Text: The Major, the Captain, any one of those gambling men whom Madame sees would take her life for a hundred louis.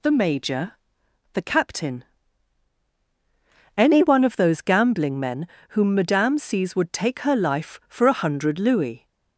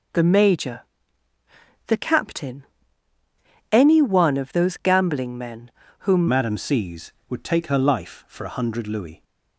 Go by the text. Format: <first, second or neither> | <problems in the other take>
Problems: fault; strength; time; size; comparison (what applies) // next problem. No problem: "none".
first | pauses between "men" and "whom"; slight; at 5.6 s; 0.30 s long; slight in the first // changes voice at "Madame"; from 6.2 s on; 3.0 s long